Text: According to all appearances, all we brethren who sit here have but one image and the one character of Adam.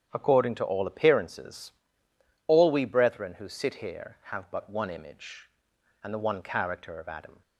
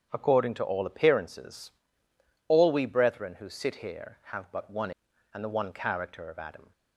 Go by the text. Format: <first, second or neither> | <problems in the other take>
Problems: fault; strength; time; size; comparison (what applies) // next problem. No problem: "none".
first | starts louder than the rest; strong; until 1.1 s; 8.5 dB; strong in the first // skips "image"; at 5.1 s